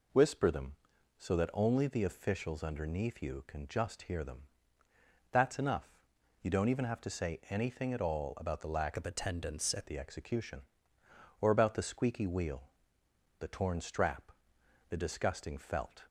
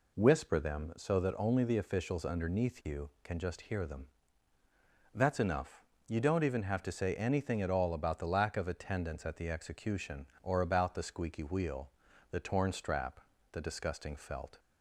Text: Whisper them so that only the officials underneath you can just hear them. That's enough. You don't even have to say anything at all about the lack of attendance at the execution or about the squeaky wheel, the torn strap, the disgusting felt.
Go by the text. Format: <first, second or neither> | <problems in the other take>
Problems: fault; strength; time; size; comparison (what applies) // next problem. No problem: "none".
second | changes voice from "of" to "at"; from 8.9 to 9.8 s; 0.9 s long